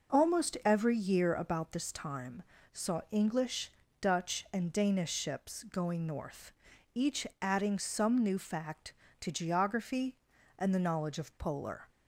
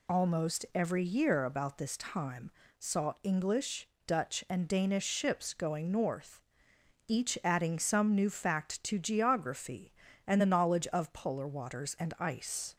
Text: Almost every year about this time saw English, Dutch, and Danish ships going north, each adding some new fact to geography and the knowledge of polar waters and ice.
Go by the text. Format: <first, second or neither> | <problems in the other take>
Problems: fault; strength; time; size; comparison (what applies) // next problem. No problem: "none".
second | pauses between "time" and "saw"; slight; at 2.4 s; 0.30 s long; slight in the second // pauses between "each" and "adding"; slight; at 7.2 s; 0.16 s long // stops before "waters and ice"; at 11.8 s